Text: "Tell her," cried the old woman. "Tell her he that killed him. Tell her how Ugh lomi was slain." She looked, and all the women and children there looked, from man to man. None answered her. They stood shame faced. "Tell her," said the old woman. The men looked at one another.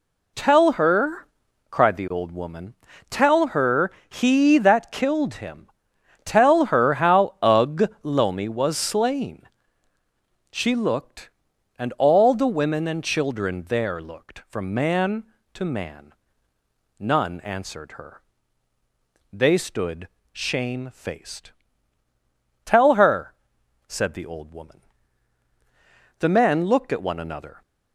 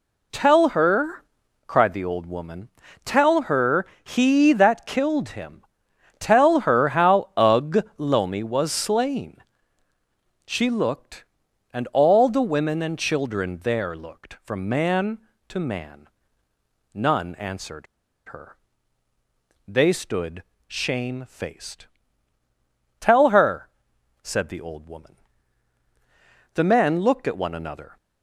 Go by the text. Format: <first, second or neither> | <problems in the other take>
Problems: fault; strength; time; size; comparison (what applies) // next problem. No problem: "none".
first | pauses between "her" and "he"; slight; at 3.8 s; 0.18 s long; slight in the first // pauses between "answered" and "her"; at 17.8 s; 0.42 s long // pauses between "stood" and "shame"; slight; at 20.4 s; 0.24 s long; slight in the first